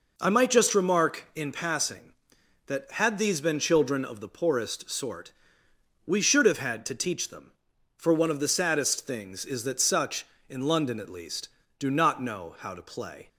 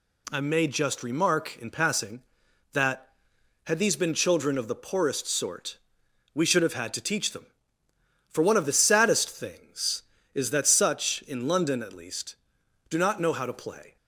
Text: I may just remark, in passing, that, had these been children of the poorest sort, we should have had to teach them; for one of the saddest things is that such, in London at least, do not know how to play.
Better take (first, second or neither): second